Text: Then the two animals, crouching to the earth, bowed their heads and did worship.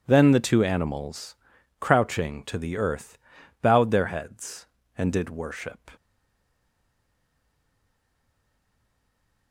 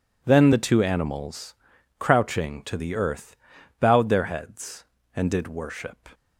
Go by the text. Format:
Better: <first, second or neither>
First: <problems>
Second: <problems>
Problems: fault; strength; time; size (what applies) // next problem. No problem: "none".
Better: second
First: stays silent after the last word; strong; from 5.9 s on; 3.6 s long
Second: none